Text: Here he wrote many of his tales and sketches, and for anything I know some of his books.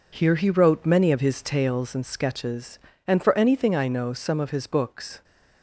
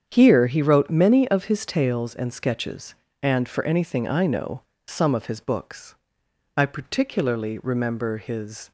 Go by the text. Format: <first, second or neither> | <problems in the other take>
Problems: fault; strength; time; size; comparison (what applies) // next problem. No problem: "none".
first | starts louder than the rest; strong; until 1.0 s; 8 dB // pauses between "know" and "some"; slight; at 4.6 s; 0.26 s long // goes on to say "I particularly remember his"; strong; from 6.5 s on; 2.1 s long